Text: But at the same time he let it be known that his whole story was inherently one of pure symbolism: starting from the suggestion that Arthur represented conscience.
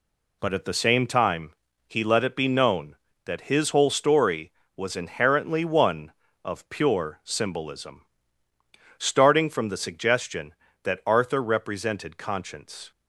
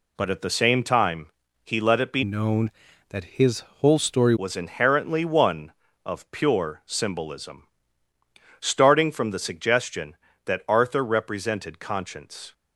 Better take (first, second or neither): first